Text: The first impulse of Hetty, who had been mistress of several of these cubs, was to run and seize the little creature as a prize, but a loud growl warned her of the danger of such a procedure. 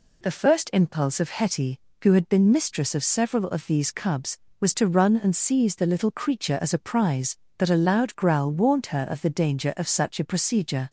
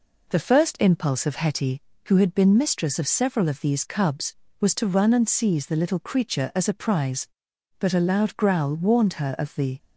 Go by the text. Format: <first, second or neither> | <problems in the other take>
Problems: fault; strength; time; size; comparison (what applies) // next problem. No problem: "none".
first | stops before "danger of such a procedure"; at 9.7 s